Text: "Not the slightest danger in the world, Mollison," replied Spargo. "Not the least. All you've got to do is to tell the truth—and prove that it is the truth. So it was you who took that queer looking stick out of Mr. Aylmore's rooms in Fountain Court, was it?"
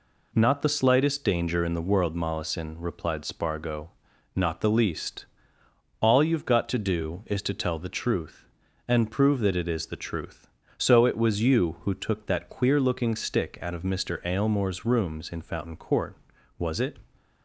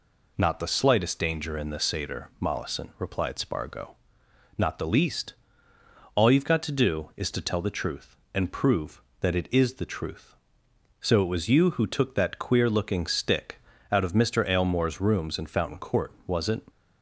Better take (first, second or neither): first